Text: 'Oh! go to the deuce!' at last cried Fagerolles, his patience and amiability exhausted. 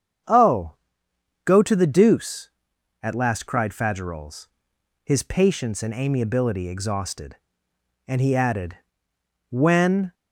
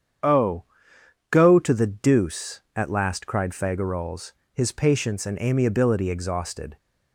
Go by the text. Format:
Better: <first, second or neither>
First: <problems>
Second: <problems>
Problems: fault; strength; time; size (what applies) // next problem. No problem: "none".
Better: second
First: starts louder than the rest; strong; until 1.9 s; 7.5 dB // goes on to say "And he added when"; strong; from 8.0 s on; 2.0 s long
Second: starts louder than the rest; strong; until 1.9 s; 8 dB